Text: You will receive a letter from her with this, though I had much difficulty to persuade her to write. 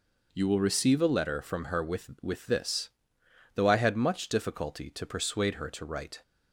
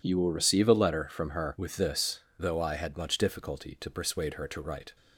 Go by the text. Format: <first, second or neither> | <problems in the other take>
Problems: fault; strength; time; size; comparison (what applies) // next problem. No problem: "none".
second | says "with" twice; at 2.2 s